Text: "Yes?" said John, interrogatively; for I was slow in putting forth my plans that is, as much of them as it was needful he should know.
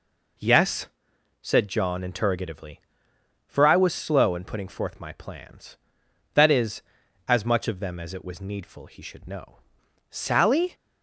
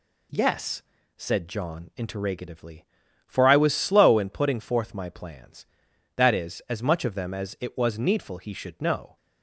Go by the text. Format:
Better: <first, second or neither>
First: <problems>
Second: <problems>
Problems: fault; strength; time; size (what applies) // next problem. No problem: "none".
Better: second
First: goes on to say "Sally"; noticeable; from 10.1 s on; 0.64 s long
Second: none